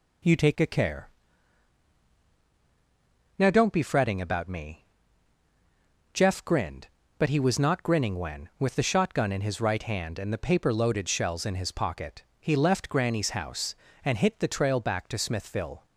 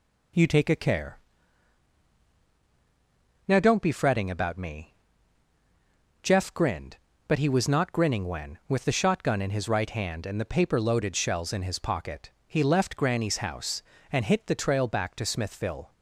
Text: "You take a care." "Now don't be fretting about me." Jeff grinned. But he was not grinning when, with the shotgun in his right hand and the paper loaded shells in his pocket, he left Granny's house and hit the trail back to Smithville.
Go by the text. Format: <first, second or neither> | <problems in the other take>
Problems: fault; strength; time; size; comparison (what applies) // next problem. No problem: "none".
neither | none